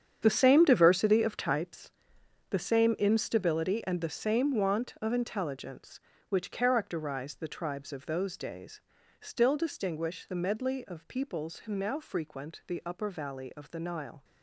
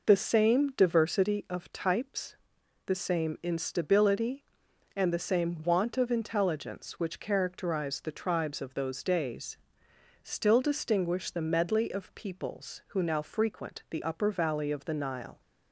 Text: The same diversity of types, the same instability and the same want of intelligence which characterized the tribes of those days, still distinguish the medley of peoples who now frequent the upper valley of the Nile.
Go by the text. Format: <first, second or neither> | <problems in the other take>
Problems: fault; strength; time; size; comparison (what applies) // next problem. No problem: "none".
second | gets quieter; strong; throughout; 13 dB